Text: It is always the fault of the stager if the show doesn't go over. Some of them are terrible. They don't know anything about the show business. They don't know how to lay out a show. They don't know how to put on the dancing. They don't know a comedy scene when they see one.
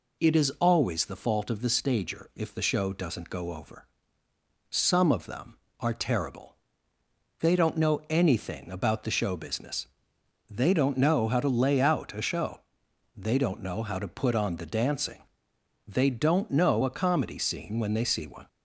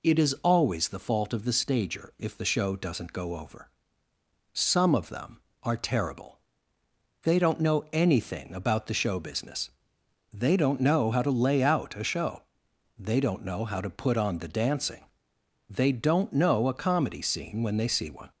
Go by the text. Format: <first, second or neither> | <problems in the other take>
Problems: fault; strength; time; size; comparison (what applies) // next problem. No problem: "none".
neither | none